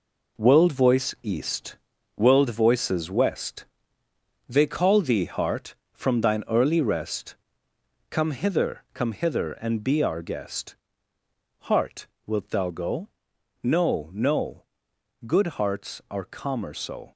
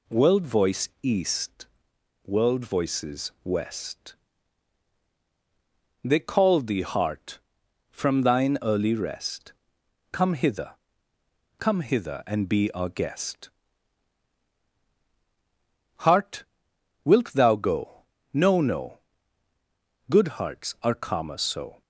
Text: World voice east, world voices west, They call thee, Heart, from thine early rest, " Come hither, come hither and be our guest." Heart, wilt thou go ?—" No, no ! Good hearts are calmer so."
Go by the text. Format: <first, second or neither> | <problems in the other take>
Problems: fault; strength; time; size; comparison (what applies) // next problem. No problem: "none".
second | gets quieter; strong; throughout; 9 dB